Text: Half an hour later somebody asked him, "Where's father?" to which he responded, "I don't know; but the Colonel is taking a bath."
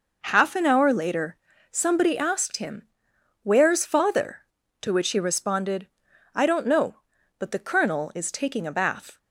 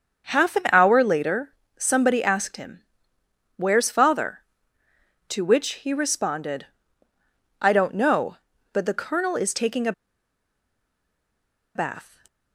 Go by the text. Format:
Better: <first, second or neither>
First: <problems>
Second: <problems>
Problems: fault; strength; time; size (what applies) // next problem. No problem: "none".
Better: first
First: pauses between "later" and "somebody"; slight; at 1.3 s; 0.35 s long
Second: starts louder than the rest; until 1.3 s; 6.5 dB // pauses between "later" and "somebody"; slight; at 1.5 s; 0.26 s long // pauses between "a" and "bath"; strong; at 9.9 s; 1.8 s long